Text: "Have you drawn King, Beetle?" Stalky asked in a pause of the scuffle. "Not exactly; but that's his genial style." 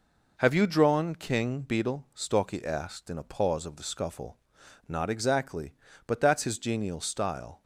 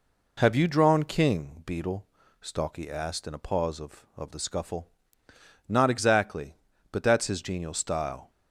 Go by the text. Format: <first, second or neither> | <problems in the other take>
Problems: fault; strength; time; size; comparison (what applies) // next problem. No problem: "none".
first | says "of" twice; at 4.1 s